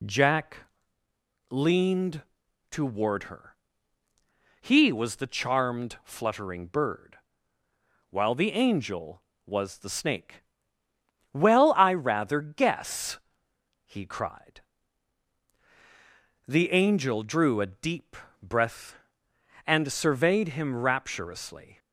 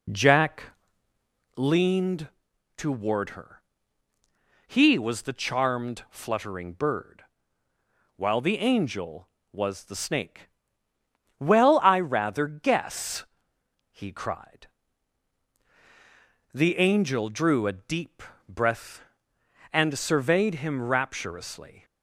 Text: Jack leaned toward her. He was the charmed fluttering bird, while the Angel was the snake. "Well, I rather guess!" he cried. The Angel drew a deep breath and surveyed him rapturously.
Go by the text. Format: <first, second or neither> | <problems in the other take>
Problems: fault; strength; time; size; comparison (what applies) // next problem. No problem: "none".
first | starts louder than the rest; slight; until 1.8 s; 3 dB // pauses between "Jack" and "leaned"; noticeable; at 0.6 s; 0.94 s long; noticeable in the first // pauses between "leaned" and "toward"; noticeable; at 2.2 s; 0.48 s long; noticeable in the first // pauses between "deep" and "breath"; slight; at 18.2 s; 0.26 s long; slight in the first